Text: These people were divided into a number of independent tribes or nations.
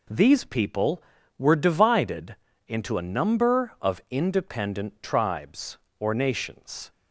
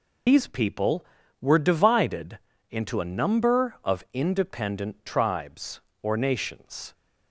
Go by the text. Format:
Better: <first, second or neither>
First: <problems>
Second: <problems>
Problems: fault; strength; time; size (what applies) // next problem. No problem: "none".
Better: first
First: pauses between "divided" and "into"; slight; at 2.3 s; 0.32 s long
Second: loses the start of "These"; at 0.2 s; 165 ms // pauses between "divided" and "into"; slight; at 2.3 s; 0.32 s long